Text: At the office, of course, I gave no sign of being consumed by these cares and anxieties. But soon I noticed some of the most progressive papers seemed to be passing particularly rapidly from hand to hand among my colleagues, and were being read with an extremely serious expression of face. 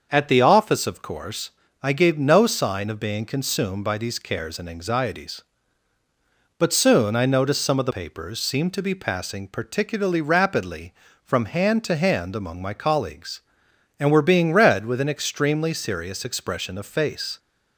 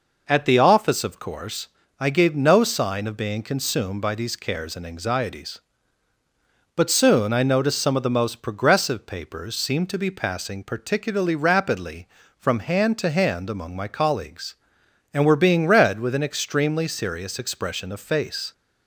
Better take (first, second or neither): second